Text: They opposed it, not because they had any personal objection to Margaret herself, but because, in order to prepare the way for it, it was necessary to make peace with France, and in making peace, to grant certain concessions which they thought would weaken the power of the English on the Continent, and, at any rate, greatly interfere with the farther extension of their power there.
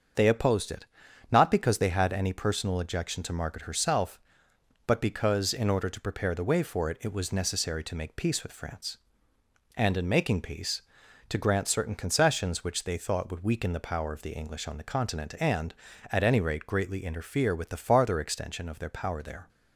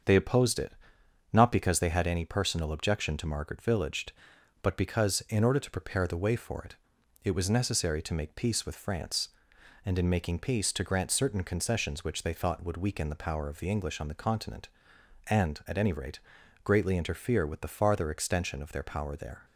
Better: first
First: starts louder than the rest; until 1.5 s; 7 dB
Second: starts louder than the rest; until 1.6 s; 7 dB // says "villaged" for "herself"; at 3.6 s

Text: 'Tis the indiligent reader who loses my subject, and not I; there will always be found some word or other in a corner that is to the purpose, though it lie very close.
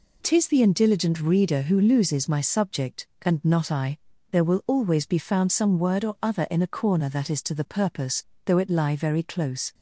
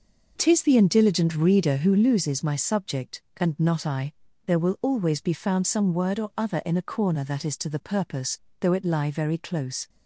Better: first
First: none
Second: starts louder than the rest; noticeable; until 2.1 s; 5.5 dB

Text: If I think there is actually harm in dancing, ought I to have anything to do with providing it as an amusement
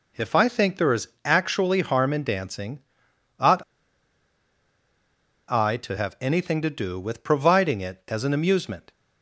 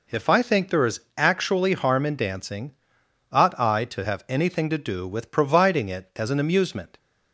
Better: second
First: pauses between "is" and "actually"; slight; at 1.0 s; 0.18 s long // pauses between "ought" and "I"; strong; at 3.6 s; 1.8 s long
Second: pauses between "is" and "actually"; slight; at 0.9 s; 0.18 s long

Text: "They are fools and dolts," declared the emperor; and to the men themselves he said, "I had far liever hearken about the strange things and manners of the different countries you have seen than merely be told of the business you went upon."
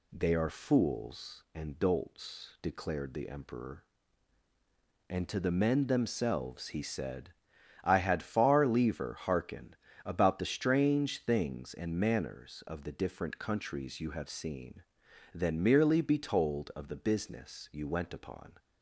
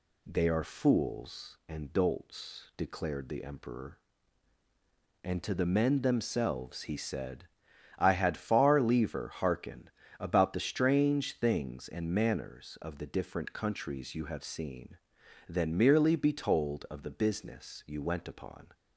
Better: neither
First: pauses between "hearken" and "about"; slight; at 9.7 s; 0.30 s long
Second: pauses between "hearken" and "about"; slight; at 9.8 s; 0.30 s long

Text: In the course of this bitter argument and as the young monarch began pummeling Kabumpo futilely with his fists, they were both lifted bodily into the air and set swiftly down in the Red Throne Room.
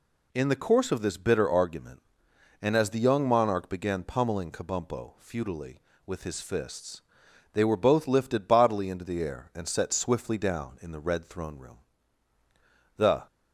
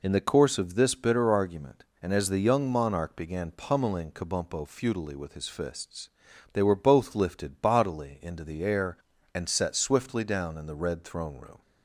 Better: second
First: goes on to say "The"; slight; from 12.9 s on; 0.26 s long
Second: none

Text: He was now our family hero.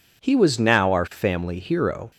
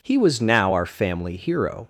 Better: neither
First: none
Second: none

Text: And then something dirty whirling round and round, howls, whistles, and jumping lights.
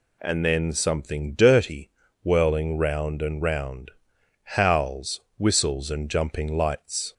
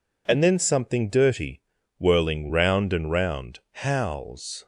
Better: first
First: pauses between "dirty" and "whirling"; slight; at 1.9 s; 0.34 s long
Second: pauses between "dirty" and "whirling"; slight; at 1.6 s; 0.36 s long // stops before "whistles and jumping lights"; at 4.6 s

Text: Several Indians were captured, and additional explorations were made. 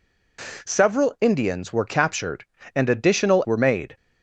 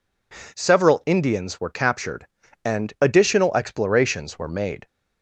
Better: second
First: skips "explorations"; at 3.4 s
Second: none

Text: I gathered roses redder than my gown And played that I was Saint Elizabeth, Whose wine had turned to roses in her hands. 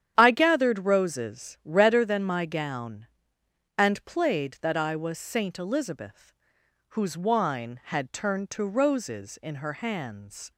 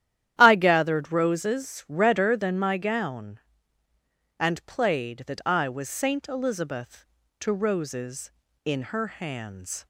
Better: first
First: starts louder than the rest; strong; until 1.1 s; 9.5 dB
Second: starts louder than the rest; strong; until 1.3 s; 11.5 dB // skips "Whose wine had turned"; at 7.2 s

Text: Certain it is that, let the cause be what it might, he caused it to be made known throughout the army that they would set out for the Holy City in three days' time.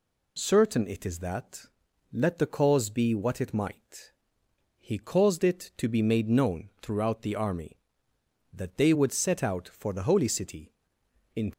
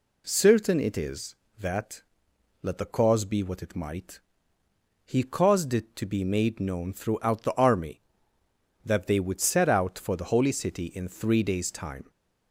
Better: second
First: stops before "three days time"; at 11.5 s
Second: none

